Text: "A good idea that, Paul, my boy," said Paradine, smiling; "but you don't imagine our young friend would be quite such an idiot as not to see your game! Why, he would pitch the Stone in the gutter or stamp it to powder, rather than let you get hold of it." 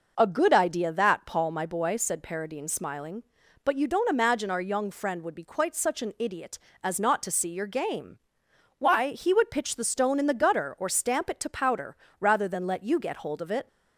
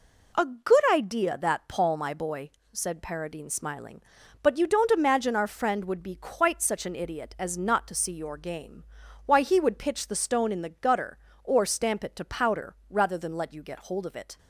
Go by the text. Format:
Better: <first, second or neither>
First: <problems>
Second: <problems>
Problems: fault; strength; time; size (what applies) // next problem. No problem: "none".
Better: first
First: none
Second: skips "young"; at 5.4 s